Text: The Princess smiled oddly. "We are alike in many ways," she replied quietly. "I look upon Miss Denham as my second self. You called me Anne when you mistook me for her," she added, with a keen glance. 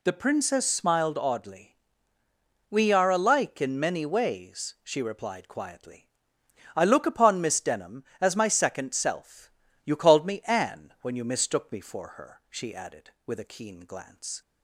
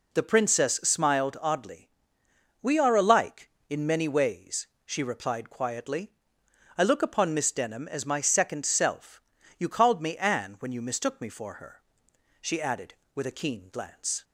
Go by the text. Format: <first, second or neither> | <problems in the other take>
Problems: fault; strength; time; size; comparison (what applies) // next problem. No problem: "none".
neither | none